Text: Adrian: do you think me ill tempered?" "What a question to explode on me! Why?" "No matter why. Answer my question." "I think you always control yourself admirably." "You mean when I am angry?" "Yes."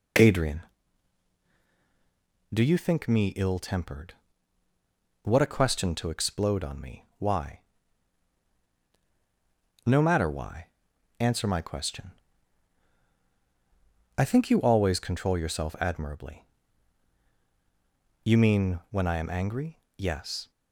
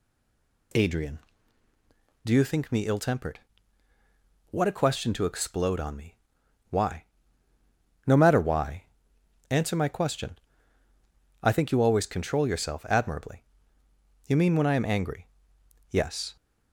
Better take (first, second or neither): first